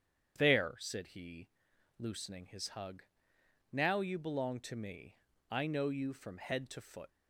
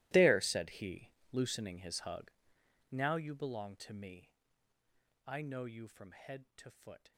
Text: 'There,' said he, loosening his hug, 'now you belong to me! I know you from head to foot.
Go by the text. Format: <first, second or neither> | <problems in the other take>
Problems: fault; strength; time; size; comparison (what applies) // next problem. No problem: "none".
first | gets quieter; strong; throughout; 19.5 dB // starts louder than the rest; strong; until 1.3 s; 17.5 dB; strong in the first